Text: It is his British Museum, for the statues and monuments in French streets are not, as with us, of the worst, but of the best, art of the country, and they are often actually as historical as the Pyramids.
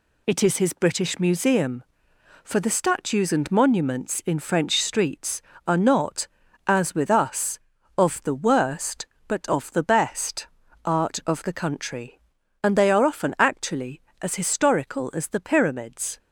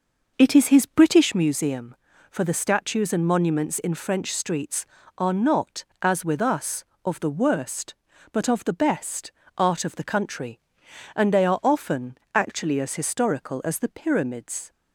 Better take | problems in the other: first | starts louder than the rest; noticeable; until 1.5 s; 5.5 dB // pauses between "often" and "actually"; slight; at 12.1 s; 0.16 s long

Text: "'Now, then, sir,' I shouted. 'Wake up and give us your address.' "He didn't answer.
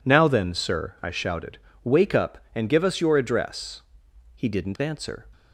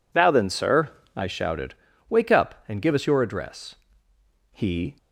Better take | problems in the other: first | stops before "didn't answer"; at 4.9 s

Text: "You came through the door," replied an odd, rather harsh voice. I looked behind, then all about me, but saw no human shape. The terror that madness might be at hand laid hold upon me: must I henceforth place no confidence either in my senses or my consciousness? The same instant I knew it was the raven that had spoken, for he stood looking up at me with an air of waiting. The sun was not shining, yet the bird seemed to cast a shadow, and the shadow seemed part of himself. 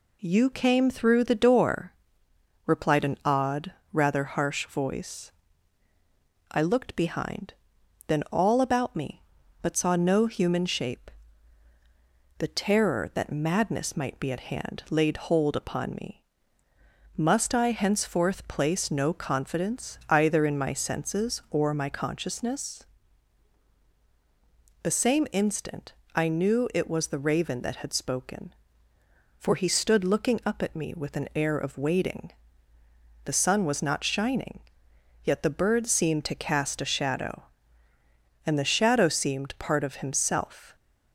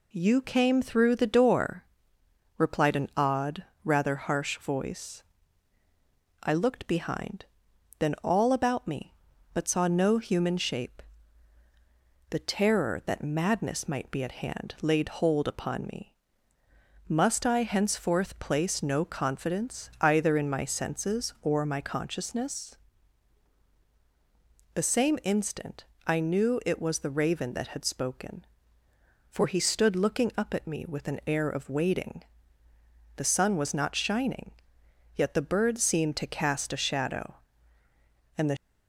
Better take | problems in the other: first | pauses between "instant" and "I"; slight; at 25.8 s; 0.20 s long; slight in the first // stops before "shadow seemed part of himself"; at 38.5 s

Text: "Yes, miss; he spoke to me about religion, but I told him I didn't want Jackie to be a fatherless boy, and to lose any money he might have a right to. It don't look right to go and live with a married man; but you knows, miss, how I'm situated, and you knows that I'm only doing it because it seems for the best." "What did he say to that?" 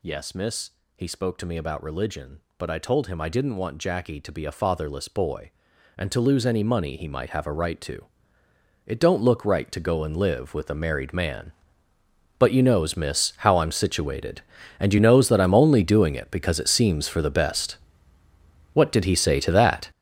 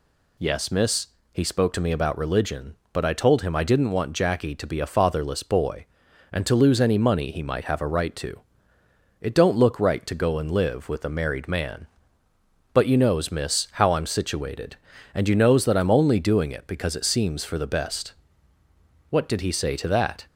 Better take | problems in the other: second | gets louder; strong; throughout; 11.5 dB

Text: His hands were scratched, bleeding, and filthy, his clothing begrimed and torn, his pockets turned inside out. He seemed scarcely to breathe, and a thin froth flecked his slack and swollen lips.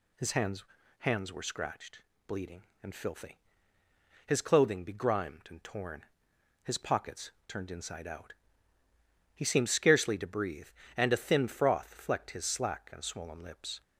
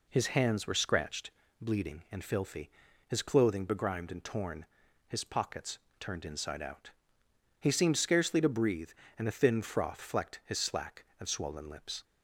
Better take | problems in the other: second | says "hands" twice; at 0.9 s // pauses between "pockets" and "turned"; slight; at 7.3 s; 0.16 s long; slight in the second

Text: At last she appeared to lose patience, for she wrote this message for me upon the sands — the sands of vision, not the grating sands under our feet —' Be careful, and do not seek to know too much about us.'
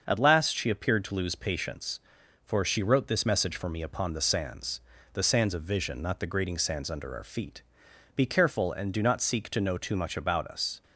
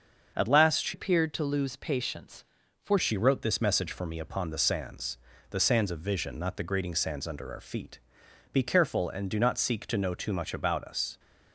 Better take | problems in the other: first | starts louder than the rest; until 1.3 s; 6.5 dB; also in the first // changes voice from "appeared" to "for"; from 0.9 to 2.9 s; 2.0 s long

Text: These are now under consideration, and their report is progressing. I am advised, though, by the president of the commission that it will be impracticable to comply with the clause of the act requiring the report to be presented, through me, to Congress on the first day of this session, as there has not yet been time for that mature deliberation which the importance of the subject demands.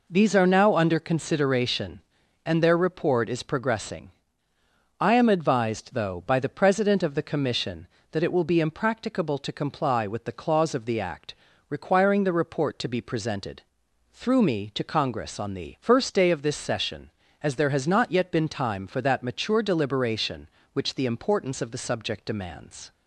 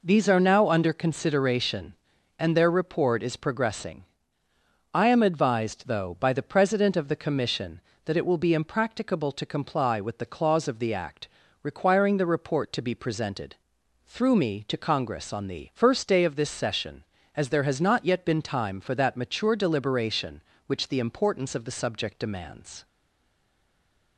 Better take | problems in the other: first | pauses between "act" and "requiring"; slight; at 11.2 s; 0.36 s long; slight in the first // stays silent after the last word; noticeable; from 22.8 s on; 1.3 s long

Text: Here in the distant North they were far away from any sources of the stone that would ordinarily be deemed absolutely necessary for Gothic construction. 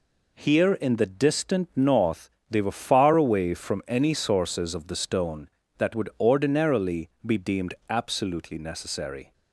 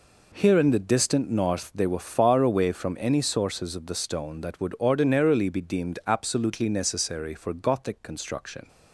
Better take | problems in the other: second | pauses between "North" and "they"; slight; at 2.2 s; 0.22 s long // stops before "for Gothic construction"; at 9.3 s

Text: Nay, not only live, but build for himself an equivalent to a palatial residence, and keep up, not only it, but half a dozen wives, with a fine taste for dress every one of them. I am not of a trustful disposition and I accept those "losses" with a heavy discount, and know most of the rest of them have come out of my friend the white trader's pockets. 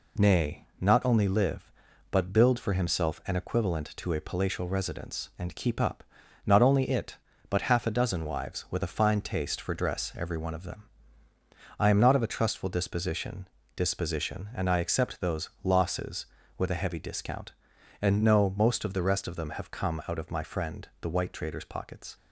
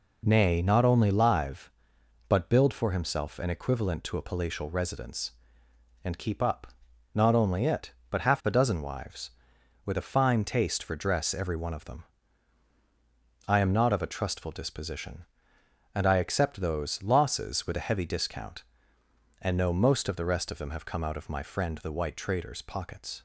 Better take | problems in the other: second | says "disposition" twice; at 13.7 s

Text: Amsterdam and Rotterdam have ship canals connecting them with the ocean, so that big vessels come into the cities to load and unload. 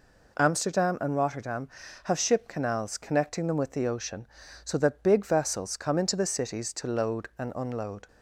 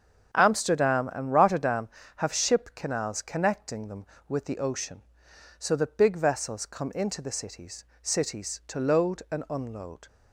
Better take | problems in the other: first | starts louder than the rest; strong; until 1.3 s; 7 dB // says "cities" twice; at 8.0 s

